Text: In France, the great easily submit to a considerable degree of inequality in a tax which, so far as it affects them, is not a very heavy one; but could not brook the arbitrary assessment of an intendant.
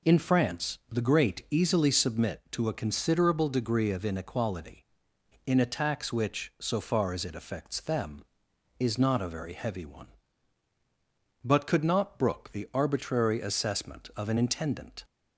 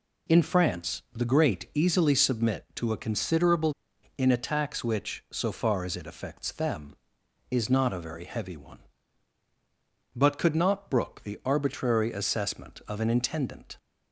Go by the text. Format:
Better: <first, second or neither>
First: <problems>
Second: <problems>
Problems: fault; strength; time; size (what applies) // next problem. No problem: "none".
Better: first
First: none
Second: skips "degree of inequality"; at 3.9 s